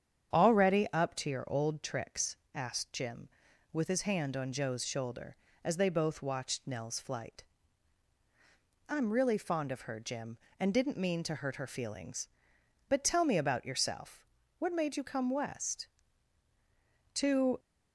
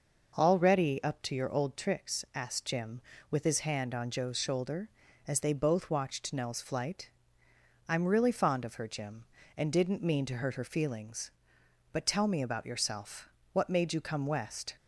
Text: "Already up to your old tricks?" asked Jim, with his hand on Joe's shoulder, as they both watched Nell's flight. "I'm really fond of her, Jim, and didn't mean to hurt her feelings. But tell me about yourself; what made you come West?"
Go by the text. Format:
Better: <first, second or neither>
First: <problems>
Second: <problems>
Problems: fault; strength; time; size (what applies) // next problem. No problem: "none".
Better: second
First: starts louder than the rest; strong; until 1.4 s; 8.5 dB // goes on to say "To"; slight; from 17.1 s on; 0.44 s long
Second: none